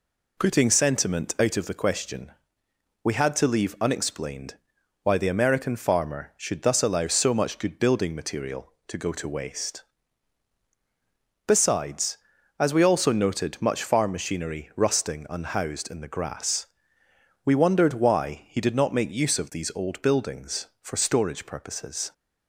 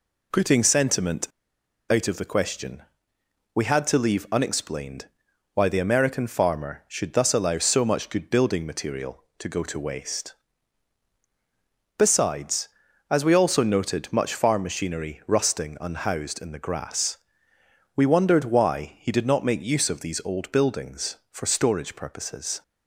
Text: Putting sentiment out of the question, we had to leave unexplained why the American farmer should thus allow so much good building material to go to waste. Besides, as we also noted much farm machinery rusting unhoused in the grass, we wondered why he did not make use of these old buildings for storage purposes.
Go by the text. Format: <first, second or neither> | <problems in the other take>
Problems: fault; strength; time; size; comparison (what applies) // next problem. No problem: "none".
first | pauses between "sentiment" and "out"; noticeable; at 1.2 s; 0.63 s long // pauses between "unexplained" and "why"; noticeable; at 5.0 s; 0.48 s long; noticeable in the first